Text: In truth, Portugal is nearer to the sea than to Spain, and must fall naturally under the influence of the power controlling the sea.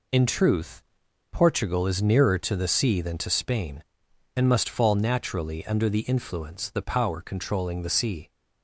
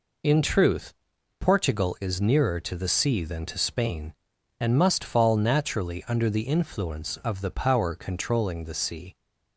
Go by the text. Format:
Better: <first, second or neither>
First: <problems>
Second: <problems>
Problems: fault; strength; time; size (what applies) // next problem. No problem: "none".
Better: second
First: skips "of"; at 6.6 s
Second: none